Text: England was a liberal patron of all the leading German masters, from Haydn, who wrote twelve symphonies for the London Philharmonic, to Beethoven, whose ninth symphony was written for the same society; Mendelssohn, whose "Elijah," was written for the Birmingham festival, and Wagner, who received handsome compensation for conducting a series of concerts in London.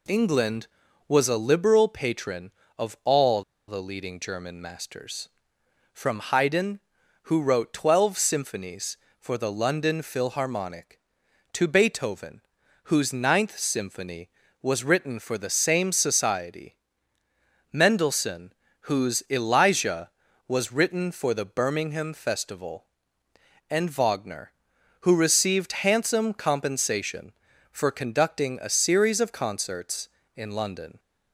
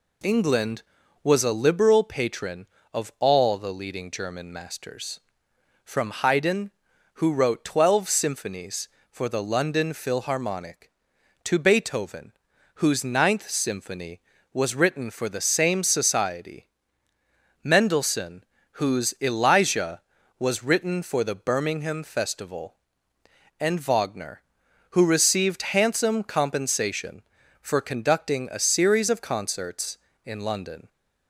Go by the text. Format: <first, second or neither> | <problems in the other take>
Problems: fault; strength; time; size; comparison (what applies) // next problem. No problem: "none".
second | pauses between "all" and "the"; slight; at 3.4 s; 0.25 s long